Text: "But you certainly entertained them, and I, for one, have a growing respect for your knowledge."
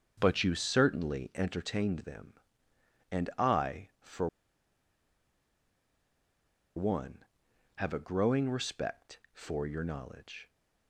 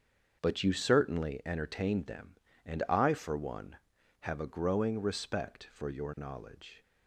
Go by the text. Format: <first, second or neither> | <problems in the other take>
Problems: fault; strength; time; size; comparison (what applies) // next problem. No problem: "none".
second | starts louder than the rest; strong; until 1.2 s; 7 dB; also in the second // pauses between "for" and "one"; strong; at 4.2 s; 2.4 s long